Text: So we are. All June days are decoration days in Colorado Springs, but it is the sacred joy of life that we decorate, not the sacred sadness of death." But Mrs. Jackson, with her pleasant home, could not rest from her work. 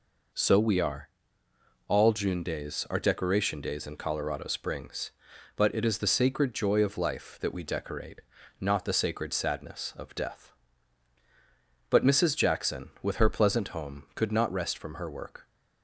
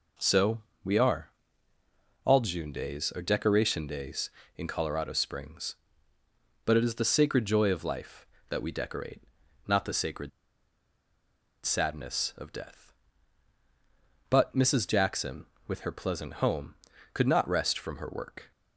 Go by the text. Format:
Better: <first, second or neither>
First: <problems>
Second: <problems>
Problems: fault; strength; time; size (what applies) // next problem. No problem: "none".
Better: first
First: none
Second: pauses between "So" and "we"; slight; at 0.5 s; 0.24 s long // pauses between "sacred" and "sadness"; strong; at 10.2 s; 1.3 s long